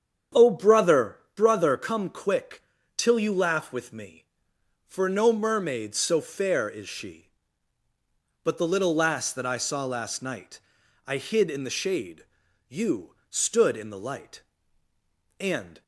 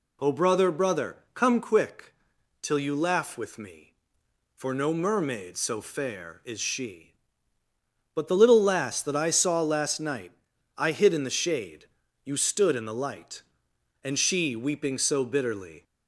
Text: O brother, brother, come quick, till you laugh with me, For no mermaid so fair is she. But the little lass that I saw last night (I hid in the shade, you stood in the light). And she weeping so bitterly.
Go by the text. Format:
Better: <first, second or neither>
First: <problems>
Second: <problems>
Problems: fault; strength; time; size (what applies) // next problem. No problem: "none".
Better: second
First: starts louder than the rest; strong; until 1.5 s; 8 dB // stops before "she weeping so bitterly"; at 15.8 s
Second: none